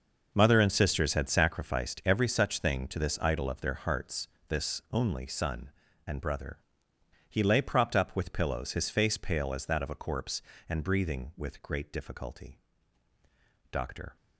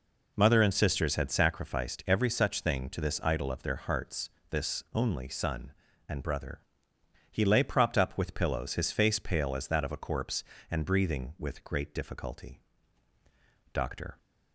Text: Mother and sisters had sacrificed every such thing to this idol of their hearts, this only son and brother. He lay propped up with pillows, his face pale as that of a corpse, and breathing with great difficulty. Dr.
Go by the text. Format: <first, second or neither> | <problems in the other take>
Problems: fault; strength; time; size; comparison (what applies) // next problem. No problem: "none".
second | gets quieter; strong; throughout; 14 dB